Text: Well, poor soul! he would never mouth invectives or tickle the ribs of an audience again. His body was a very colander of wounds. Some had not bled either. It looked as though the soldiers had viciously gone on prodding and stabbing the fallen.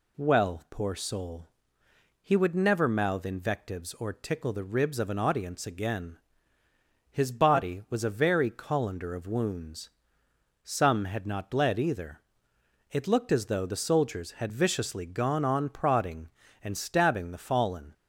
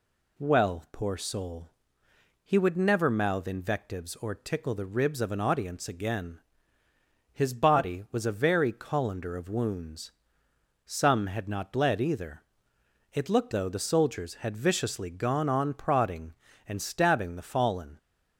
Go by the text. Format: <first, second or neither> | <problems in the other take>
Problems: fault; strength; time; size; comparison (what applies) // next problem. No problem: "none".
first | skips "as"; at 13.5 s